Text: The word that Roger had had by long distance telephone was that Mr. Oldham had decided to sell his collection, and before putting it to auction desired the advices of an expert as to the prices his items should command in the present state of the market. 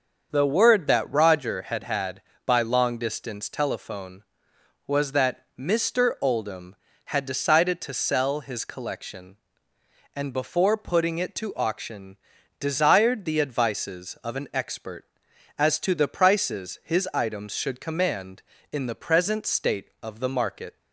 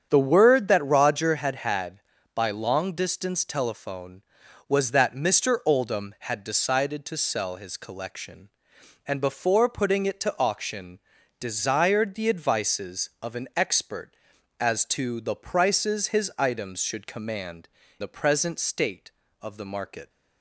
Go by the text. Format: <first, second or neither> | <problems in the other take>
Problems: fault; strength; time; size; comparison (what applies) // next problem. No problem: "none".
first | starts louder than the rest; strong; until 1.1 s; 7.5 dB; also in the first // pauses between "auction" and "desired"; at 10.9 s; 0.40 s long; also in the first // skips "in"; at 17.8 s